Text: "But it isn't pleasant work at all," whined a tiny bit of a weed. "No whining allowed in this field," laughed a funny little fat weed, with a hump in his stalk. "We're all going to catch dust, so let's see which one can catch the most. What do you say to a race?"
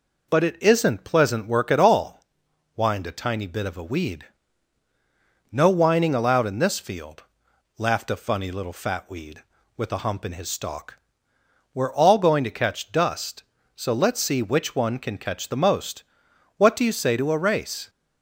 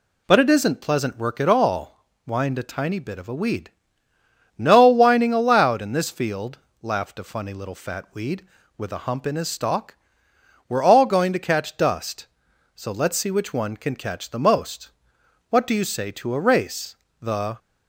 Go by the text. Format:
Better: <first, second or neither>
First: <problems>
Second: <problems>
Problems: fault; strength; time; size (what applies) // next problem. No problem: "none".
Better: first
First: none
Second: goes on to say "The"; slight; from 17.2 s on; 0.38 s long